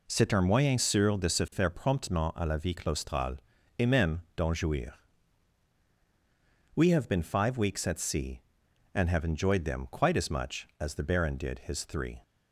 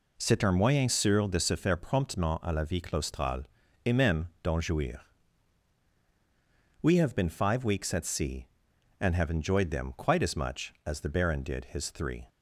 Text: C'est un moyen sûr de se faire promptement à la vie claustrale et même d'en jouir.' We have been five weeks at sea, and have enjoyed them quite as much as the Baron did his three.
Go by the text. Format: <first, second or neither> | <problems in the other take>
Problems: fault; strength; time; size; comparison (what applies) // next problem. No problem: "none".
neither | pauses between "claustrale" and "et"; the same in both